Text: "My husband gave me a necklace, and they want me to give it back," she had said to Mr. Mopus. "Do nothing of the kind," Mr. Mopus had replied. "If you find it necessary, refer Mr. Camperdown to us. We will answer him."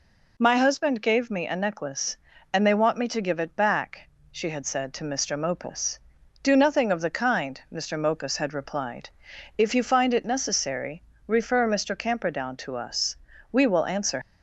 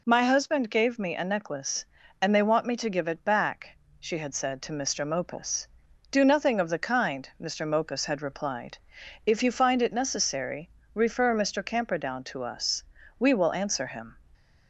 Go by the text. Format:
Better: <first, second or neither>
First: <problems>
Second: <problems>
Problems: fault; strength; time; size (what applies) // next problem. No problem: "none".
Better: second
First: stops before "him"; at 14.2 s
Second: none